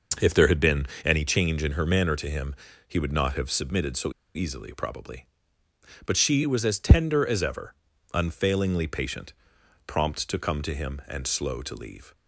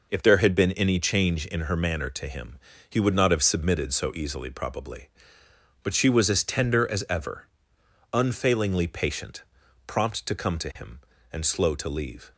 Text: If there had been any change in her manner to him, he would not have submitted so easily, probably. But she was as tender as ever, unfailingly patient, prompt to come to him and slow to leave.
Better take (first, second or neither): second